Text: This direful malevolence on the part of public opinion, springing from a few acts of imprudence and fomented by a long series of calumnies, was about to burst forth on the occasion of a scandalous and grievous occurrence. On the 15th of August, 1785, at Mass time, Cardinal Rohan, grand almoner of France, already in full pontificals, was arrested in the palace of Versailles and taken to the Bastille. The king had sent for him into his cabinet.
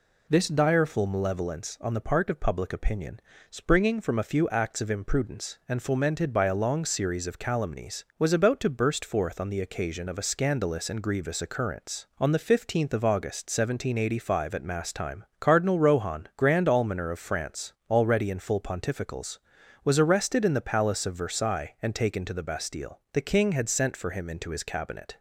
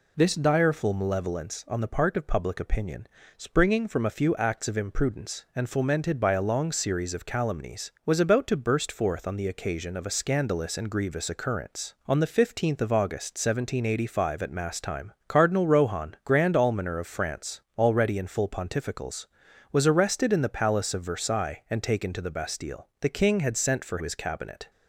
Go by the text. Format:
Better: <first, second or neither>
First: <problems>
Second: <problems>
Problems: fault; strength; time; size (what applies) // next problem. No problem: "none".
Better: first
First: none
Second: skips "him into"; at 24.0 s